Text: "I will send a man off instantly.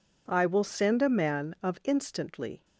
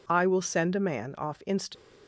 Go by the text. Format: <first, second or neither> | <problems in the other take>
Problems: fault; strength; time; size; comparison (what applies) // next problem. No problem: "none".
second | says "of" for "off"; at 1.6 s